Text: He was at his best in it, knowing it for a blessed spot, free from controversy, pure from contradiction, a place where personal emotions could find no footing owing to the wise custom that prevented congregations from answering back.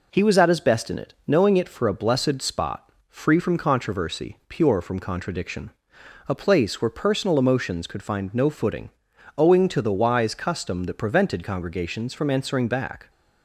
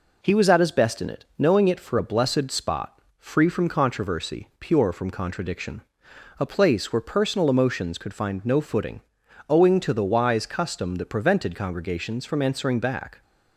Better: neither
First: pauses between "footing" and "owing"; noticeable; at 8.9 s; 0.49 s long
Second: pauses between "footing" and "owing"; noticeable; at 9.0 s; 0.50 s long

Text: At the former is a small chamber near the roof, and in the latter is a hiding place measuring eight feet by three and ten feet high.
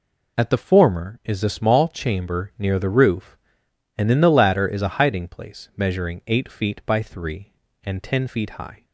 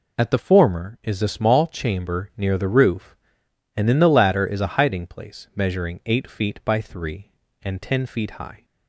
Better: neither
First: none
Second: none

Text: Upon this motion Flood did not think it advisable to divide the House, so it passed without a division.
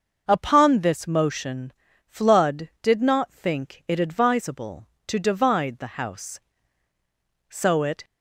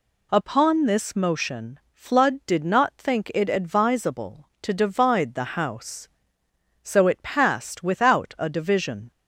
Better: second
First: starts louder than the rest; noticeable; until 1.2 s; 6 dB // pauses between "motion" and "Flood"; slight; at 1.7 s; 0.34 s long // stops before "passed without a division"; at 8.0 s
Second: pauses between "motion" and "Flood"; slight; at 1.7 s; 0.15 s long

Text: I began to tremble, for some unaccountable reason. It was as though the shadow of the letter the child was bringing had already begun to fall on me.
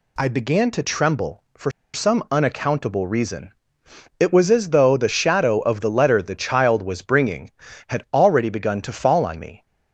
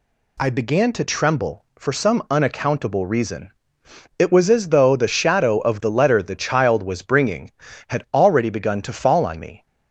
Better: second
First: pauses between "for" and "some"; slight; at 1.6 s; 0.24 s long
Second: none

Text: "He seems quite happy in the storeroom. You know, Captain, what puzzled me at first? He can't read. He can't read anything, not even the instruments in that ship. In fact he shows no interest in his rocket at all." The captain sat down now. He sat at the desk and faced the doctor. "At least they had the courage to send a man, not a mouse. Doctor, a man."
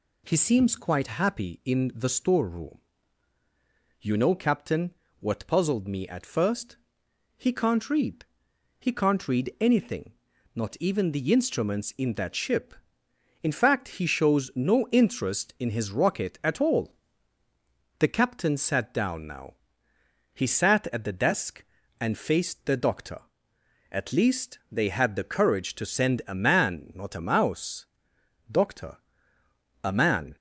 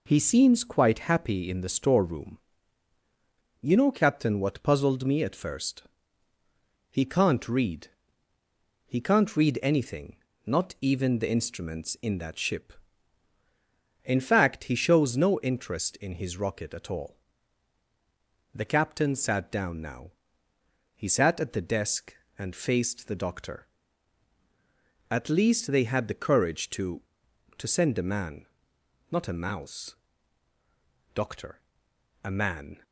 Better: first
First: none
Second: says "to" twice; at 27.5 s

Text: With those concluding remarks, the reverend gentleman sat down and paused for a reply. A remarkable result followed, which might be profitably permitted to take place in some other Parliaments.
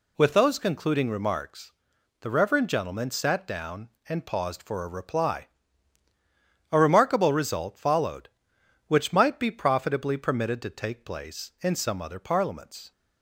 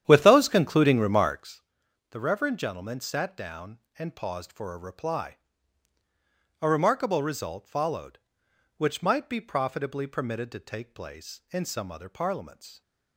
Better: first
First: none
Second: starts louder than the rest; strong; until 1.6 s; 10 dB

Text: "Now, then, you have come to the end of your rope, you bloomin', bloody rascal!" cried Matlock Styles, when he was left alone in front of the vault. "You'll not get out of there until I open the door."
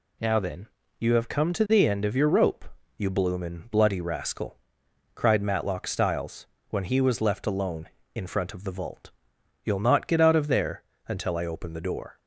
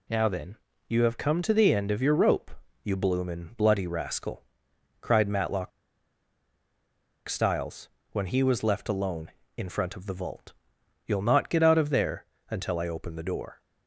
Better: first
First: pauses between "there" and "until"; slight; at 10.8 s; 0.24 s long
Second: pauses between "Matlock" and "Styles"; strong; at 5.7 s; 1.5 s long // pauses between "there" and "until"; slight; at 12.2 s; 0.24 s long

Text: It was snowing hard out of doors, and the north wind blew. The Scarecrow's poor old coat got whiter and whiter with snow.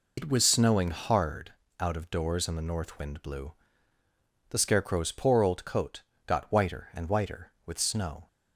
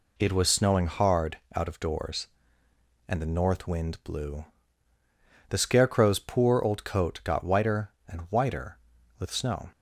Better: second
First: loses the start of "It"; at 0.1 s; 80 ms // pauses between "hard" and "out"; slight; at 1.5 s; 0.30 s long // pauses between "coat" and "got"; slight; at 6.0 s; 0.24 s long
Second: pauses between "hard" and "out"; slight; at 1.3 s; 0.18 s long

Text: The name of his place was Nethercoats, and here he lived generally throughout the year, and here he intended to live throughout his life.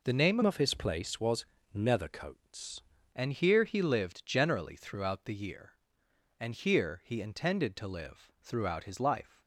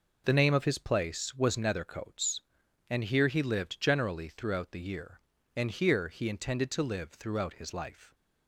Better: second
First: changes voice from "of" to "Nethercoats"; from 0.4 to 2.8 s; 2.4 s long // pauses between "was" and "Nethercoats"; slight; at 1.4 s; 0.28 s long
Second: none

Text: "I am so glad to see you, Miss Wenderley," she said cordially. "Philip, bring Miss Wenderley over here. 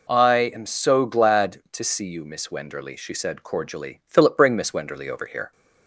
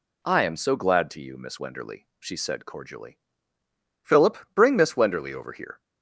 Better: first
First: none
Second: skips "see"; at 1.2 s

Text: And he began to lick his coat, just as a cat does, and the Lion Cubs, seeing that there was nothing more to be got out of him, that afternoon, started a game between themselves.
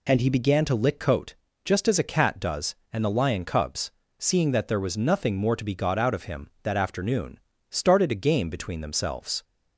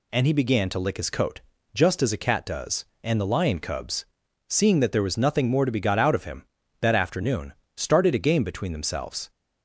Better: second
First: skips "his"; at 0.9 s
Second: none

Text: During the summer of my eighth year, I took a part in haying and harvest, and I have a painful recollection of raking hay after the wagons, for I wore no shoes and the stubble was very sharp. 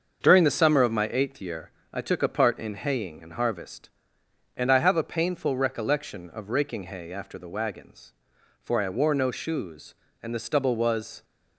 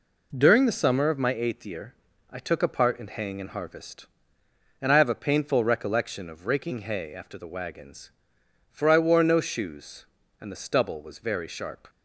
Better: second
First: starts louder than the rest; until 1.2 s; 6.5 dB // stops before "very sharp"; at 11.2 s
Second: none

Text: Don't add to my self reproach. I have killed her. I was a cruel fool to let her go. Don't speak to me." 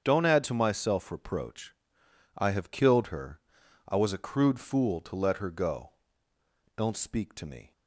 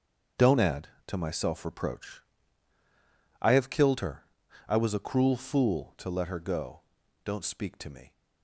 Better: second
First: starts louder than the rest; strong; until 1.0 s; 7.5 dB // says "crude" for "cruel"; at 4.1 s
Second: starts louder than the rest; until 1.5 s; 6.5 dB

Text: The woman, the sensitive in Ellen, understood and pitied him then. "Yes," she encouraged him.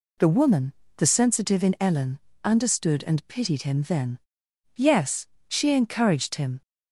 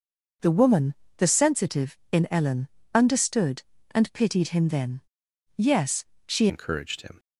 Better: first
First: none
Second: changes voice at "encouraged"; from 6.4 s on; 0.7 s long

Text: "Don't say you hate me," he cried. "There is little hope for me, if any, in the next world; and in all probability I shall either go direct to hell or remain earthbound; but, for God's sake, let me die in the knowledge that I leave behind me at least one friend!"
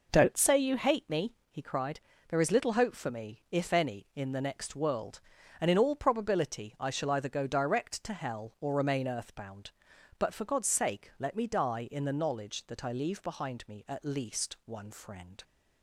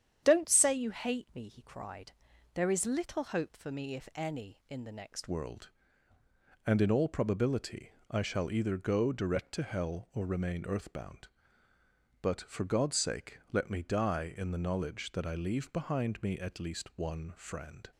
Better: first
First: none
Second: starts louder than the rest; strong; until 1.2 s; 9 dB // changes voice at "world"; from 5.2 s on; 12.7 s long // pauses between "probability" and "I"; slight; at 7.9 s; 0.18 s long

